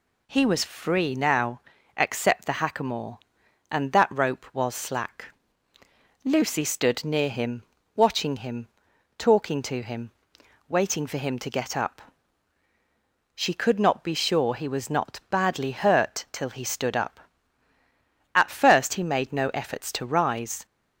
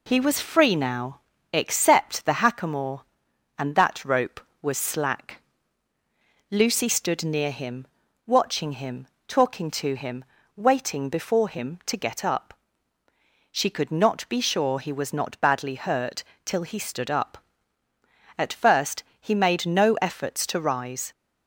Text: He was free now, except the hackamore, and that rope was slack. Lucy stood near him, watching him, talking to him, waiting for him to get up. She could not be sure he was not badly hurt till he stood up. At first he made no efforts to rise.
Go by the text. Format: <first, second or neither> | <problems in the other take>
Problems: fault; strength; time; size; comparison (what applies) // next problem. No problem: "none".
first | says "before" for "for"; at 11.0 s // pauses between "hurt" and "till"; slight; at 16.2 s; 0.22 s long // pauses between "first" and "he"; slight; at 19.0 s; 0.16 s long